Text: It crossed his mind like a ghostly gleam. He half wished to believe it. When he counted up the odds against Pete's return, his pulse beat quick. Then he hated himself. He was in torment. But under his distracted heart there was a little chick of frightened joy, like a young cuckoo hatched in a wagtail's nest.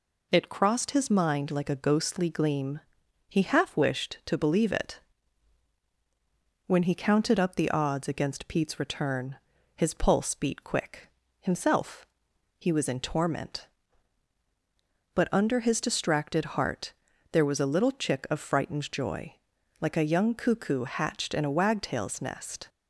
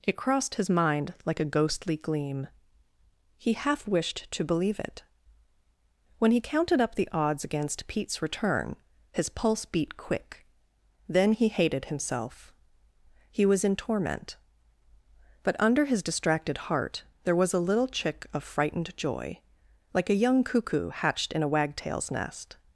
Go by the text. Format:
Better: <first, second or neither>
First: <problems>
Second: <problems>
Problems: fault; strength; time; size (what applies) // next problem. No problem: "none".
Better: second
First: skips "Then he hated"; at 11.2 s // pauses between "heart" and "there"; at 16.9 s; 0.40 s long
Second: pauses between "heart" and "there"; slight; at 17.0 s; 0.22 s long